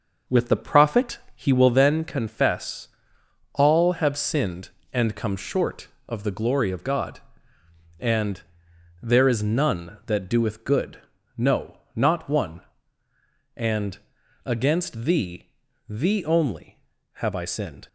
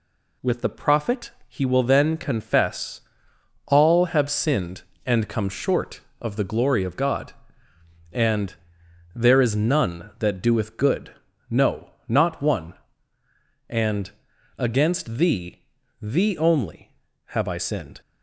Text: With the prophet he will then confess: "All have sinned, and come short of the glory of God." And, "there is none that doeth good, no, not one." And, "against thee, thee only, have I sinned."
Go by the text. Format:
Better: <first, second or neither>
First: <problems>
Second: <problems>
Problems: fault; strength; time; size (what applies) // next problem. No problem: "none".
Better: second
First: starts louder than the rest; noticeable; until 1.9 s; 6 dB // pauses between "prophet" and "he"; slight; at 1.1 s; 0.18 s long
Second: pauses between "prophet" and "he"; slight; at 1.3 s; 0.18 s long